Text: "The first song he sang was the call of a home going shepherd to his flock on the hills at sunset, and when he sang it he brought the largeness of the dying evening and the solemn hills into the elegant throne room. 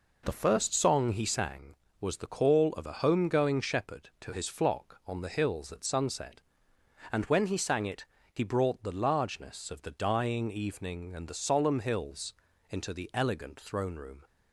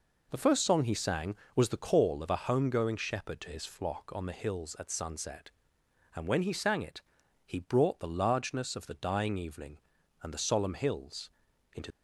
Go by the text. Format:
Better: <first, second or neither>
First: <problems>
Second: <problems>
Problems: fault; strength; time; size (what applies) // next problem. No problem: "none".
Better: first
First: pauses between "it" and "he"; slight; at 8.0 s; 0.26 s long // pauses between "hills" and "into"; slight; at 12.3 s; 0.36 s long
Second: pauses between "it" and "he"; at 7.0 s; 0.44 s long // pauses between "hills" and "into"; at 11.2 s; 0.44 s long // stops before "the elegant throne room"; at 11.9 s